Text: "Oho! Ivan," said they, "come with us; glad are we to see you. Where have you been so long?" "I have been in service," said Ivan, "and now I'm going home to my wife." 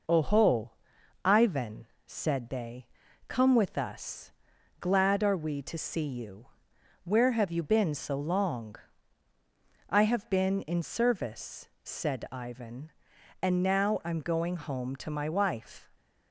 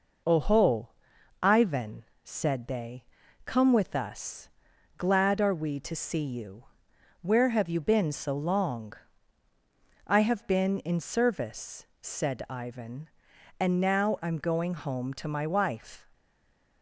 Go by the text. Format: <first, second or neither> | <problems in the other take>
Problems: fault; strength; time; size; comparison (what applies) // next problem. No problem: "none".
first | stays silent after the last word; slight; from 16.1 s on; 0.7 s long